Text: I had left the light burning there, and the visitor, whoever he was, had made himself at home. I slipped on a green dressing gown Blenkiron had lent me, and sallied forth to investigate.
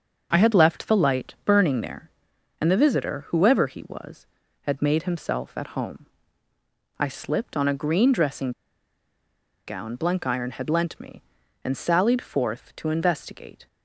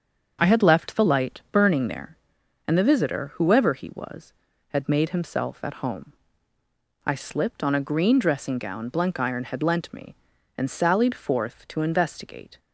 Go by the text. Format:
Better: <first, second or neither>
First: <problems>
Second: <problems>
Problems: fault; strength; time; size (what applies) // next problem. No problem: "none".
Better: second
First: starts louder than the rest; until 1.3 s; 6.5 dB // pauses between "dressing" and "gown"; at 8.5 s; 1.1 s long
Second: starts louder than the rest; until 1.5 s; 6.5 dB